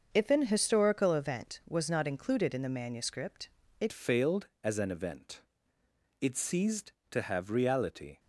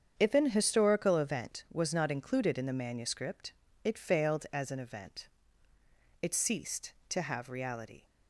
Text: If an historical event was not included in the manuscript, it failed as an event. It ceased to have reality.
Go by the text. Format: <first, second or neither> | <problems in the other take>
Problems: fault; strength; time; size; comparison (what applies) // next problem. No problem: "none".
second | starts louder than the rest; until 1.1 s; 6.5 dB; strong in the second // changes voice at "failed"; from 3.9 s on; 4.2 s long